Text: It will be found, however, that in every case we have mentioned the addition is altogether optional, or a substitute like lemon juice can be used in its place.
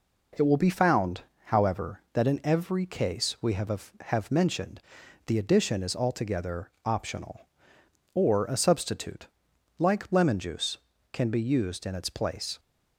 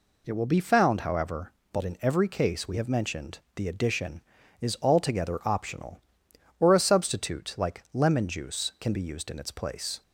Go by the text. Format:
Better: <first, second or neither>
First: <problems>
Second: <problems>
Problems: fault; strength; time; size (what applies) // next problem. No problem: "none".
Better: second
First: says "have" twice; at 3.9 s // pauses between "mentioned" and "the"; noticeable; at 4.7 s; 0.48 s long // pauses between "altogether" and "optional"; slight; at 6.6 s; 0.15 s long // pauses between "substitute" and "like"; noticeable; at 9.2 s; 0.50 s long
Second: pauses between "mentioned" and "the"; slight; at 3.3 s; 0.16 s long